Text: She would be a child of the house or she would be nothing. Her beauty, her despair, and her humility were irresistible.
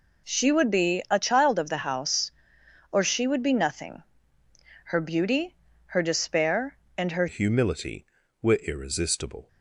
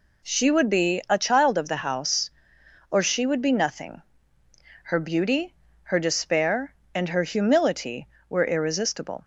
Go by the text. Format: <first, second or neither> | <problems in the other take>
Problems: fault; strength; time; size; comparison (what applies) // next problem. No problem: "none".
second | changes voice at "humility"; from 7.2 s on; 2.2 s long